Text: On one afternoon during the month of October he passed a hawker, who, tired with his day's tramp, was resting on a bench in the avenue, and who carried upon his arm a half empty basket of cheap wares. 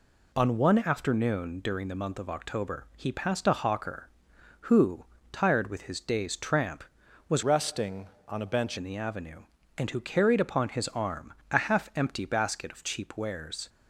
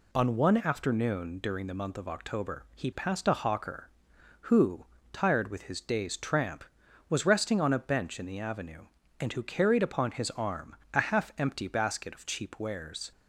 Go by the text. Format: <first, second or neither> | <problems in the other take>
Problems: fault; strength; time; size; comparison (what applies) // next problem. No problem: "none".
second | changes voice from "resting" to "bench"; from 7.4 to 8.7 s; 1.3 s long // pauses between "arm" and "a"; slight; at 11.3 s; 0.18 s long; slight in the second